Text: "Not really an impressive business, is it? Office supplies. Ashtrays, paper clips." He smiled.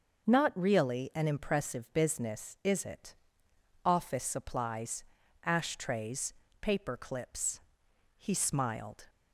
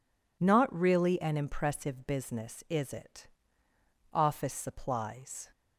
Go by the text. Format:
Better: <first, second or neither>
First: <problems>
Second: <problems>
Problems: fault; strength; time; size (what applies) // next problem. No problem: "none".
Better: first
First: none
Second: stops before "Ashtrays paper clips He smiled"; at 5.5 s